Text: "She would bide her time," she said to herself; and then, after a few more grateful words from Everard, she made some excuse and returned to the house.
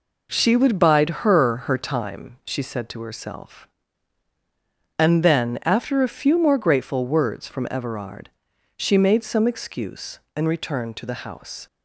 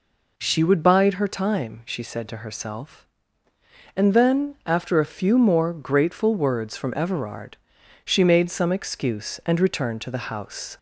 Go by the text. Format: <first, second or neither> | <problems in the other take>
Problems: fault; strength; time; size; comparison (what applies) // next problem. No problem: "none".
second | says "her" twice; at 1.6 s